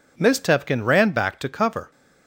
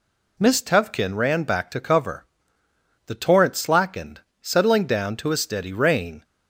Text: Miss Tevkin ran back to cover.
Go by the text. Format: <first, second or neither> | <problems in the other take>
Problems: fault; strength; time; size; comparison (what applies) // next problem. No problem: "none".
first | goes on to say "The torrent slackened settling down to a steady rain"; strong; from 3.0 s on; 3.1 s long